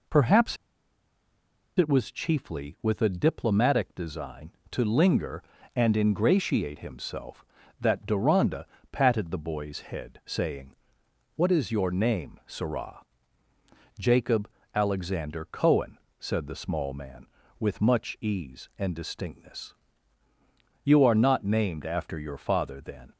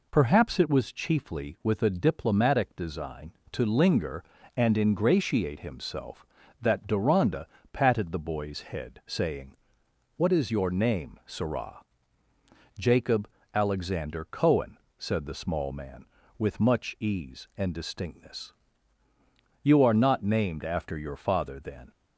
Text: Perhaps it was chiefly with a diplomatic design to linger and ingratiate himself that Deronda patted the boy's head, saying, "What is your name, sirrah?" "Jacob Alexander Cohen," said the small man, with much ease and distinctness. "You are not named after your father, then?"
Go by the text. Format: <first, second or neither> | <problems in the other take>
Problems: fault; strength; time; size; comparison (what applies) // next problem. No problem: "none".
second | pauses between "Perhaps" and "it"; at 0.5 s; 1.2 s long // pauses between "Deronda" and "patted"; slight; at 8.6 s; 0.26 s long; slight in the second // pauses between "Jacob" and "Alexander"; slight; at 14.4 s; 0.26 s long; slight in the second